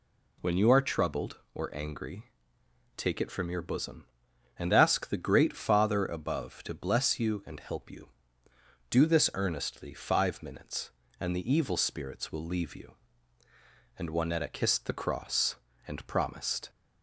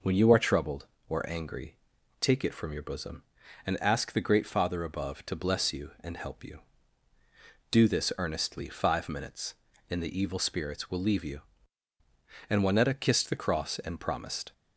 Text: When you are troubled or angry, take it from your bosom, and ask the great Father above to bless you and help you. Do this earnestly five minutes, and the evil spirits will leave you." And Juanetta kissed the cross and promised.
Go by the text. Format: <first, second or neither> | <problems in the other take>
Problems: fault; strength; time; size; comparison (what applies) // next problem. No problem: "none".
neither | none